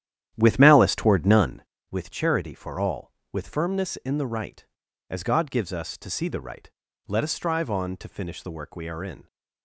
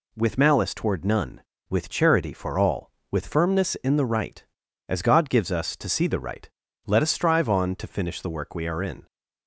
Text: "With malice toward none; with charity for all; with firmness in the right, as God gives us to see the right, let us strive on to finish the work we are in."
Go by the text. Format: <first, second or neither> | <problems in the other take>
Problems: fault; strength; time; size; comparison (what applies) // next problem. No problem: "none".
second | starts louder than the rest; strong; until 1.7 s; 11 dB